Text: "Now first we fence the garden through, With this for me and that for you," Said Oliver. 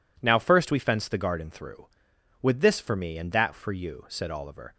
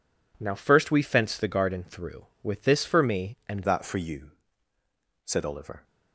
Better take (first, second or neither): first